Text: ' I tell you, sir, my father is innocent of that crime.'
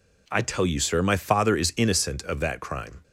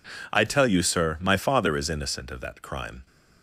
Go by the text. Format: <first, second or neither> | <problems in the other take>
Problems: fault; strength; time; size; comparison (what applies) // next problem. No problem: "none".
neither | none